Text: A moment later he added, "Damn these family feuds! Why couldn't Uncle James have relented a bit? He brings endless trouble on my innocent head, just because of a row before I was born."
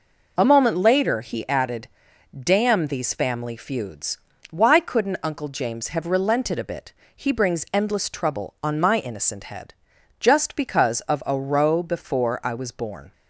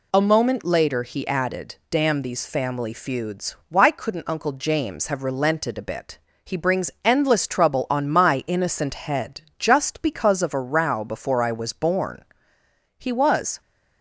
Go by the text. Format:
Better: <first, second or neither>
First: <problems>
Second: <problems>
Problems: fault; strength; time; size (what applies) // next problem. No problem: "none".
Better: first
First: none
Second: goes on to say "He was"; noticeable; from 12.9 s on; 0.62 s long